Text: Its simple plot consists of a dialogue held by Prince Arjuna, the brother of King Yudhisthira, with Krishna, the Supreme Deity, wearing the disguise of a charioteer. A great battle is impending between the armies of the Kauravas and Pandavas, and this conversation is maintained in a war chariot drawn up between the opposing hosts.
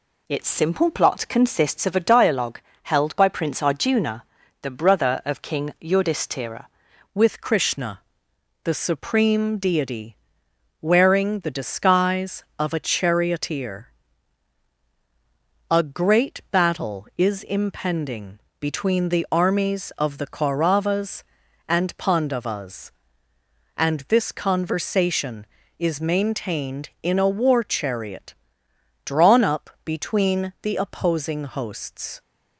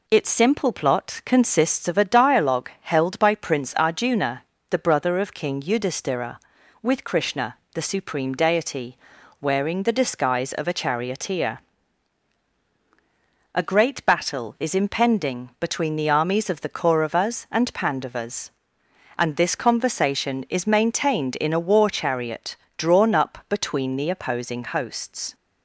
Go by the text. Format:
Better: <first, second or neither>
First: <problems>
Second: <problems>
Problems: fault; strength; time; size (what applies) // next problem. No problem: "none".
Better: second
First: pauses between "dialogue" and "held"; slight; at 2.5 s; 0.24 s long // changes voice at "with"; from 7.1 s on; 25.1 s long // pauses between "impending" and "between"; slight; at 18.3 s; 0.20 s long // pauses between "chariot" and "drawn"; noticeable; at 28.3 s; 0.72 s long // pauses between "up" and "between"; slight; at 29.6 s; 0.16 s long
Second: pauses between "chariot" and "drawn"; slight; at 22.5 s; 0.20 s long